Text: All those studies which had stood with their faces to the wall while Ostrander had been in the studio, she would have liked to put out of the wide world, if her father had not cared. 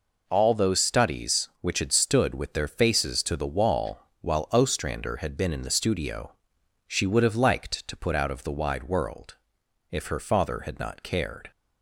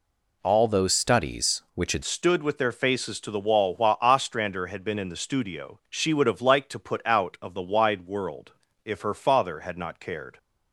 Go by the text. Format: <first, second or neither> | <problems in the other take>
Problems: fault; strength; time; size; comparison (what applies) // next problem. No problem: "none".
first | changes voice at "stood"; from 2.0 s on; 8.3 s long